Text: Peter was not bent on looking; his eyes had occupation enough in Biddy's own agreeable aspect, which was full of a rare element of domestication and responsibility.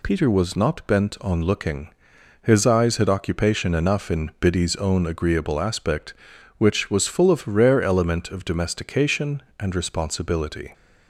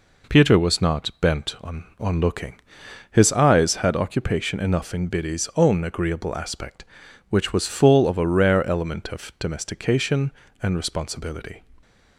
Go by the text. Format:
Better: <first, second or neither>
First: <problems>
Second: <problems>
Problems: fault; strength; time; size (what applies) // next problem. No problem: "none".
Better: first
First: none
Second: says "on" twice; at 1.9 s